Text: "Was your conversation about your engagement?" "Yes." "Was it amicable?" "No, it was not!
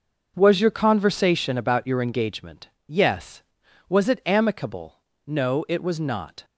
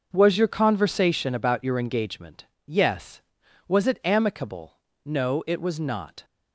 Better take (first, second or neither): neither